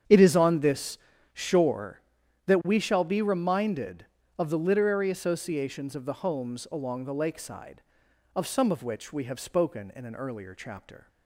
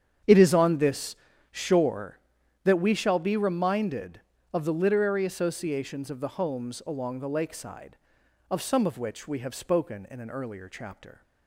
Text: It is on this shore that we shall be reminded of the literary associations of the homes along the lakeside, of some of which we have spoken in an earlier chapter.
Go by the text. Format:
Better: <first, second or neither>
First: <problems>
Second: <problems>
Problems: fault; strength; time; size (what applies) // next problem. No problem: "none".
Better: neither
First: starts louder than the rest; strong; until 1.4 s; 8 dB // pauses between "this" and "shore"; slight; at 0.9 s; 0.34 s long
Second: starts louder than the rest; strong; until 1.5 s; 8 dB // pauses between "this" and "shore"; slight; at 1.1 s; 0.34 s long